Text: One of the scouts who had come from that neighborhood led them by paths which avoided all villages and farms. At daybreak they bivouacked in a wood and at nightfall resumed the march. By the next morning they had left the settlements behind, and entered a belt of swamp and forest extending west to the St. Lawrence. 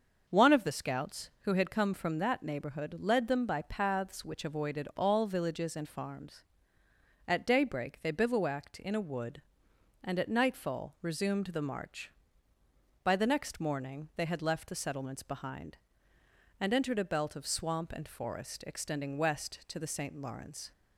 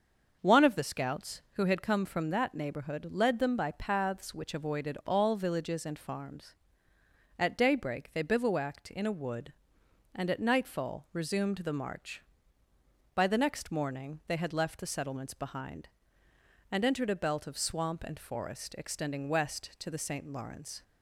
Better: neither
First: starts louder than the rest; until 1.3 s; 6.5 dB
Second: starts louder than the rest; until 1.4 s; 6.5 dB

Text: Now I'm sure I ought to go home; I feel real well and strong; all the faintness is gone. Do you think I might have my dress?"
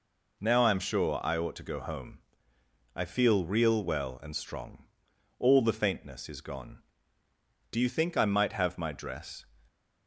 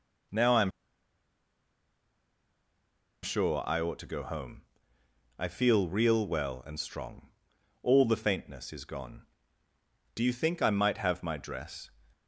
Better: first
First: none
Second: pauses between "I'm" and "sure"; strong; at 0.7 s; 2.5 s long

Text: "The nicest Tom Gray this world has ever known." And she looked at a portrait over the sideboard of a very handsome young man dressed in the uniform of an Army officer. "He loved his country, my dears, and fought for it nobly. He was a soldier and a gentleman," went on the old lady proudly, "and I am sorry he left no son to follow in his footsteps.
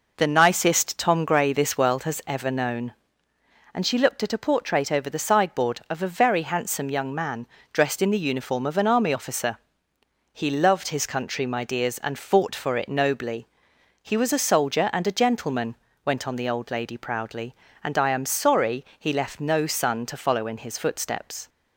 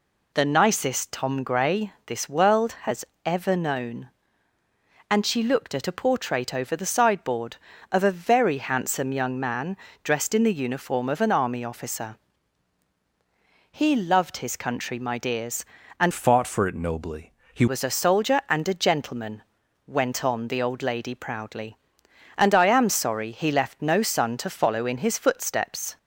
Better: first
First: pauses between "man" and "dressed"; slight; at 7.4 s; 0.24 s long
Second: pauses between "has" and "ever"; slight; at 3.0 s; 0.22 s long // pauses between "man" and "dressed"; slight; at 9.7 s; 0.28 s long // changes voice from "fought" to "He"; from 16.1 to 17.6 s; 1.5 s long

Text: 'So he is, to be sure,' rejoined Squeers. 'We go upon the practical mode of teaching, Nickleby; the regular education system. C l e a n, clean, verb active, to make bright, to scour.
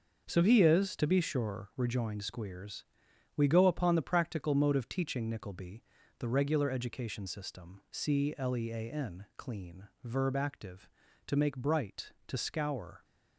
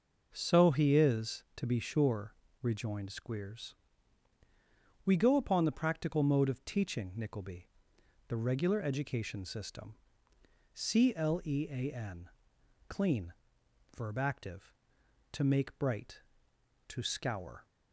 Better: second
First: gets quieter; strong; throughout; 9.5 dB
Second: none

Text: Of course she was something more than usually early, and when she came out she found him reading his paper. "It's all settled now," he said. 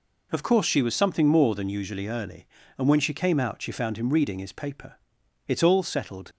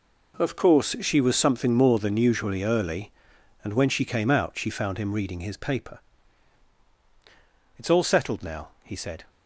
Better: second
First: stops before "now he said"; at 6.3 s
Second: none

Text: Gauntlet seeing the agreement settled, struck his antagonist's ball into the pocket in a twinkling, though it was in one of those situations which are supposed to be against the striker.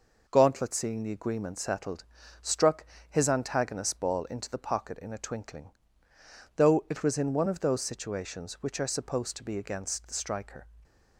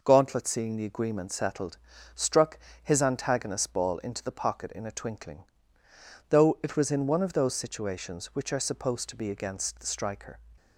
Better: neither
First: pauses between "struck" and "his"; slight; at 2.8 s; 0.24 s long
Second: pauses between "struck" and "his"; slight; at 2.5 s; 0.24 s long

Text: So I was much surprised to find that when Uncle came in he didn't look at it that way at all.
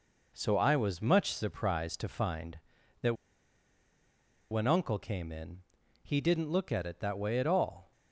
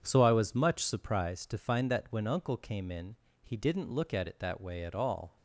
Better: second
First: pauses between "that" and "when"; strong; at 3.1 s; 1.3 s long // pauses between "in" and "he"; at 5.6 s; 0.38 s long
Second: pauses between "in" and "he"; slight; at 3.1 s; 0.30 s long

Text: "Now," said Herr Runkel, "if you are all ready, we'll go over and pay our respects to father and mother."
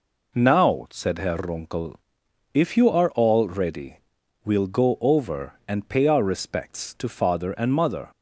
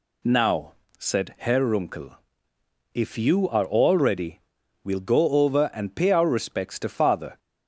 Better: first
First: none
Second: stops before "and mother"; at 7.3 s

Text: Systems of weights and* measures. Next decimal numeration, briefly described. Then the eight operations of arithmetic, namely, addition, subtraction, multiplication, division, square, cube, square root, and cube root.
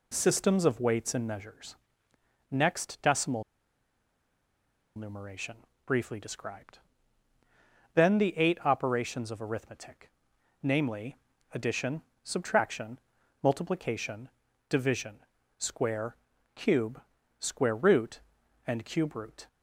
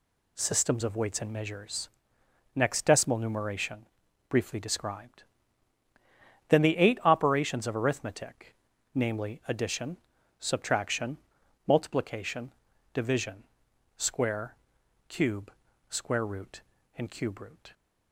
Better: second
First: pauses between "decimal" and "numeration"; strong; at 3.4 s; 1.5 s long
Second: none

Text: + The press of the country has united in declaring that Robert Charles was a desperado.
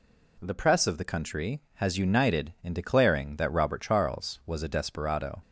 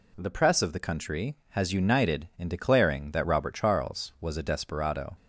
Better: neither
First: none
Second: none

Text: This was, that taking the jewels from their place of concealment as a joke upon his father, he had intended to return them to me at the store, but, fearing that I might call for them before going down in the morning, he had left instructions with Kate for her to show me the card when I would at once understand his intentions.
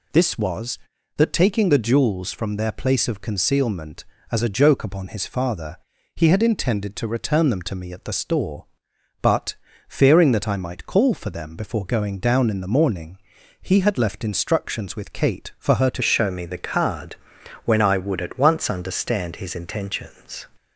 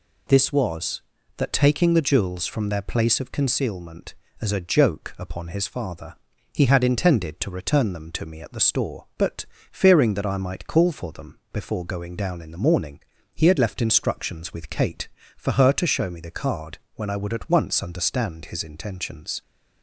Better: second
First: changes voice at "show"; from 16.0 s on; 4.4 s long // pauses between "card" and "when"; noticeable; at 17.1 s; 0.48 s long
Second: pauses between "card" and "when"; slight; at 16.7 s; 0.18 s long

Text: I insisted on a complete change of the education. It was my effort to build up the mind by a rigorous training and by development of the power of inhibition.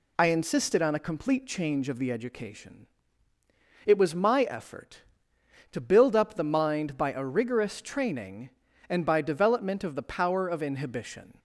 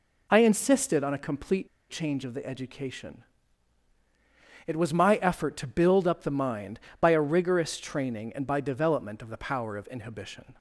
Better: first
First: none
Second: pauses between "complete" and "change"; slight; at 1.6 s; 0.21 s long

